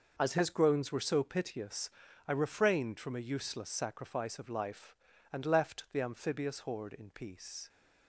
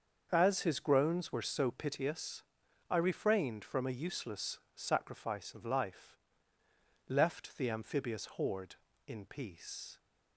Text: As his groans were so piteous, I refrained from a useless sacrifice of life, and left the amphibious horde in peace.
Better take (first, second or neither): first